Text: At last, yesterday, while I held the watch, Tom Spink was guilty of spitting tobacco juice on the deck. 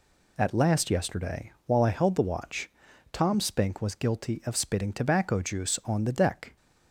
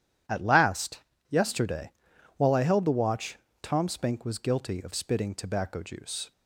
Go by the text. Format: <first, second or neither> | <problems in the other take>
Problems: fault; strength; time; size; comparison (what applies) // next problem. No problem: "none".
first | starts louder than the rest; strong; until 1.6 s; 10.5 dB // stops before "on the deck"; at 6.3 s